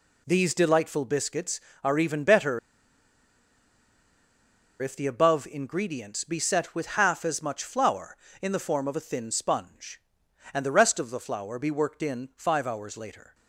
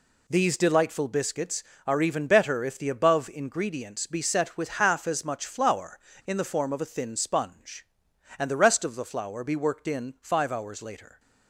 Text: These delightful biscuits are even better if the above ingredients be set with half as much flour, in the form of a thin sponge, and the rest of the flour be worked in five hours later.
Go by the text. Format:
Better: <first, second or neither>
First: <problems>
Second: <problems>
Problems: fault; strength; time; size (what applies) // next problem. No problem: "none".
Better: second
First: pauses between "better" and "if"; strong; at 2.5 s; 2.2 s long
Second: none